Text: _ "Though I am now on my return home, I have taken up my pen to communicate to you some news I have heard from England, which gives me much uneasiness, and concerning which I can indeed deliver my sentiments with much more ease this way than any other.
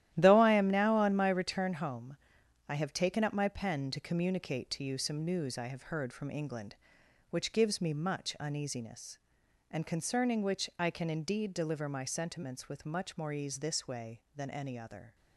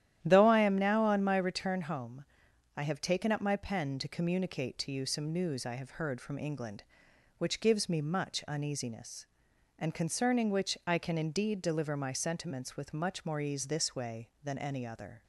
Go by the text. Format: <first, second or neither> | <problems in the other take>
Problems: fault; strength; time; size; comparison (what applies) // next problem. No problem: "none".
second | gets quieter; strong; throughout; 10 dB // starts louder than the rest; strong; until 1.1 s; 12.5 dB; strong in the second